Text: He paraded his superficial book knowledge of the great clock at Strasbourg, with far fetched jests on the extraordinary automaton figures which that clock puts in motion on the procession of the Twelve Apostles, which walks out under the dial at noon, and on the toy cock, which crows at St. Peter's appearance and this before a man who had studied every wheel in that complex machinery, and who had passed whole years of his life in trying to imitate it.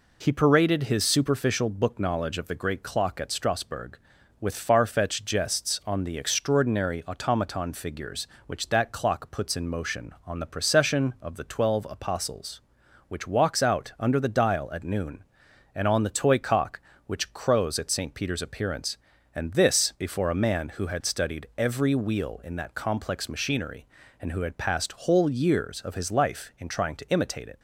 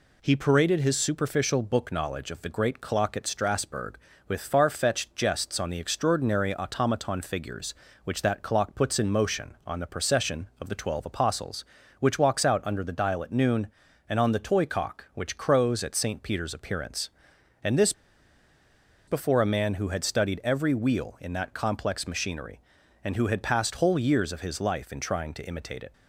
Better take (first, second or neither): first